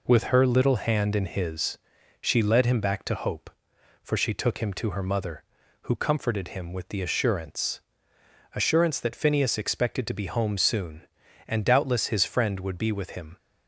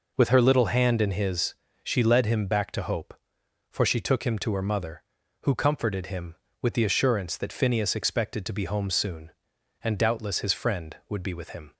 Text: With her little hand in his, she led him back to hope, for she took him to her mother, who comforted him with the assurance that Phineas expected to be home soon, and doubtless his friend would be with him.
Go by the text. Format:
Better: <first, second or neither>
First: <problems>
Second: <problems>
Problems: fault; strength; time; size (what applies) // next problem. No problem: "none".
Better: second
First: says "assurance" twice; at 8.5 s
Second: none